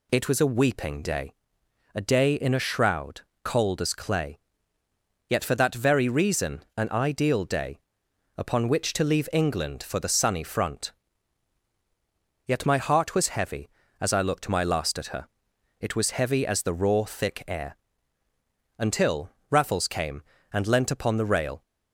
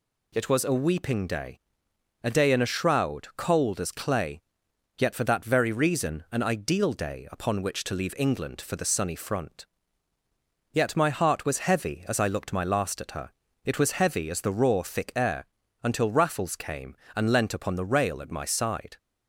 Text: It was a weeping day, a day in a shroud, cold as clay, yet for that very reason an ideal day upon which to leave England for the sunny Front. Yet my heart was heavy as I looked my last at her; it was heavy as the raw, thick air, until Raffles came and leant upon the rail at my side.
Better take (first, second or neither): second